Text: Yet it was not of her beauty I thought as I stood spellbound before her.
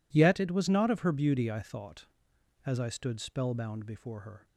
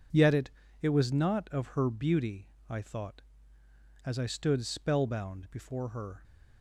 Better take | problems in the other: first | says "it" twice; at 0.8 s // pauses between "beauty" and "I"; slight; at 2.4 s; 0.20 s long

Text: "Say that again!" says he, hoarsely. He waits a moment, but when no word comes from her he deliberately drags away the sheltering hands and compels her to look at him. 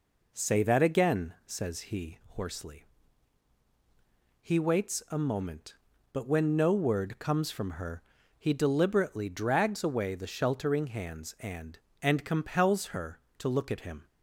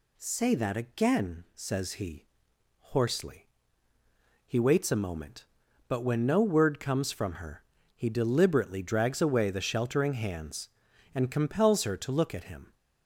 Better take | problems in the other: second | pauses between "her" and "he"; slight; at 8.0 s; 0.36 s long; slight in the second // says "and" twice; at 12.0 s

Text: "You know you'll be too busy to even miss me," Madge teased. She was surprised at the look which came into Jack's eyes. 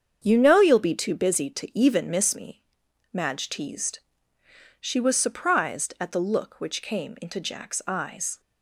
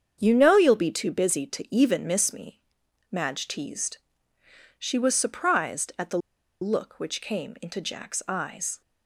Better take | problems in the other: first | starts louder than the rest; strong; until 1.2 s; 7.5 dB; strong in the first // pauses between "the" and "look"; at 6.1 s; 0.43 s long

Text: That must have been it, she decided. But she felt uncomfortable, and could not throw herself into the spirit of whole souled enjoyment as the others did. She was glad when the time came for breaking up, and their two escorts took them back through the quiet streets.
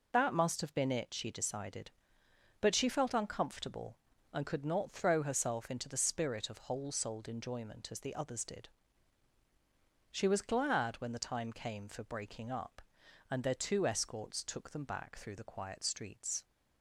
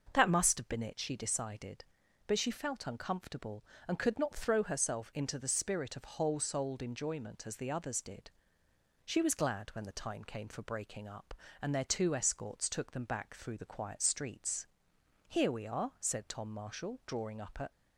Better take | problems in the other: first | starts louder than the rest; noticeable; until 1.1 s; 6 dB // goes on to say "Here we are said Tom Marshall drawing up at"; strong; from 15.2 s on; 2.4 s long

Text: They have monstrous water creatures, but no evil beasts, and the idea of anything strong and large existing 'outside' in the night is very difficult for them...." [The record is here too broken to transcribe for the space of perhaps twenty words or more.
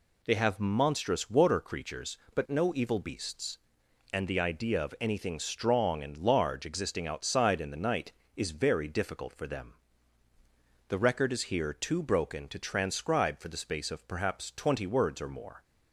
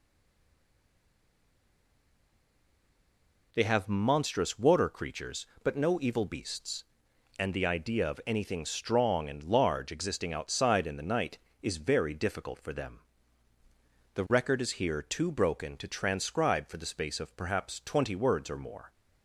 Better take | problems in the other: first | stays silent before the first word; strong; until 3.5 s; 3.5 s long

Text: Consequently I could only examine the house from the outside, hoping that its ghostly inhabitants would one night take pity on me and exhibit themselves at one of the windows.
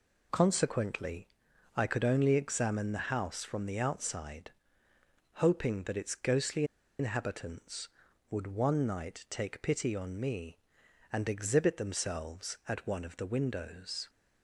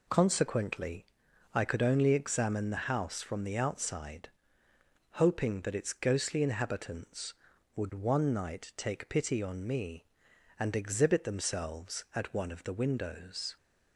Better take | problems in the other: second | pauses between "Consequently" and "I"; noticeable; at 1.2 s; 0.48 s long; noticeable in the second // pauses between "ghostly" and "inhabitants"; slight; at 6.6 s; 0.35 s long

